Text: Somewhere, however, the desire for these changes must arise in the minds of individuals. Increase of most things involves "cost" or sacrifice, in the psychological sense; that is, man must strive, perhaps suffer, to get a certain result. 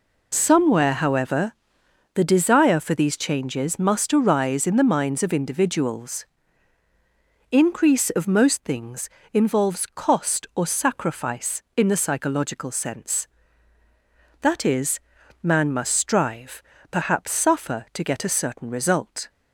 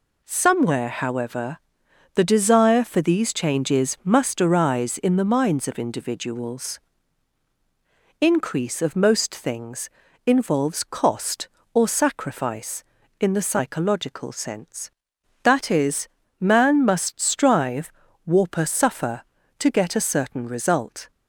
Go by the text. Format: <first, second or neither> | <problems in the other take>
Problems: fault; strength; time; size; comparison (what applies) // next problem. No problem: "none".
first | pauses between "things" and "involves"; at 9.8 s; 0.38 s long; slight in the first // says "warper" for "perhaps"; at 18.2 s